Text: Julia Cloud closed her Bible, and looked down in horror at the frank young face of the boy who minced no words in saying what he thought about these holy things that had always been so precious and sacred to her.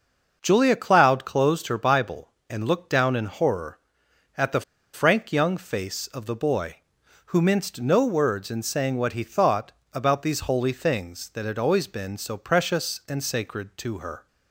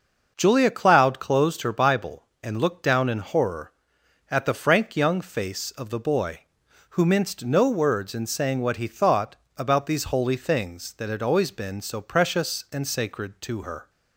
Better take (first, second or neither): second